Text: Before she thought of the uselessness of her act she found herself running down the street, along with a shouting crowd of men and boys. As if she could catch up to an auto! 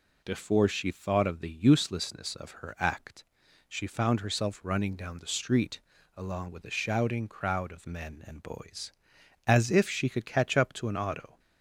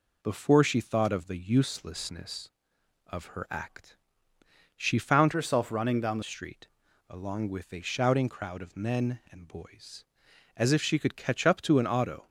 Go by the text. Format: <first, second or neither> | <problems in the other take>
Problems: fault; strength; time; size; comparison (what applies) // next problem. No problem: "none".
first | pauses between "act" and "she"; noticeable; at 3.9 s; 0.80 s long; also in the first // changes voice from "herself" to "the"; from 5.3 to 6.2 s; 0.9 s long